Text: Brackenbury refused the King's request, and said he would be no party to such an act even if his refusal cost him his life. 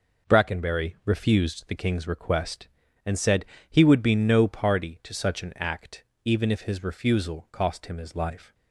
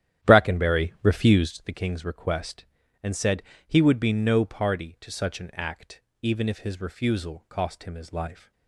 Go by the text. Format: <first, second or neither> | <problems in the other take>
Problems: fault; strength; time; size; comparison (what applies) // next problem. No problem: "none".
first | starts louder than the rest; strong; until 1.6 s; 11 dB // pauses between "said" and "he"; slight; at 3.4 s; 0.24 s long; slight in the first // pauses between "act" and "even"; slight; at 6.0 s; 0.20 s long; slight in the first